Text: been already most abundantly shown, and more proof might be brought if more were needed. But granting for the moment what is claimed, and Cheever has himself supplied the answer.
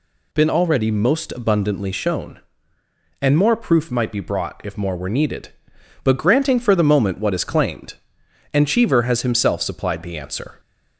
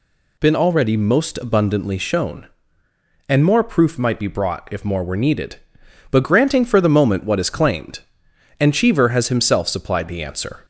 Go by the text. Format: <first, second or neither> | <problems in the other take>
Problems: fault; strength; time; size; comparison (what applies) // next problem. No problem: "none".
neither | none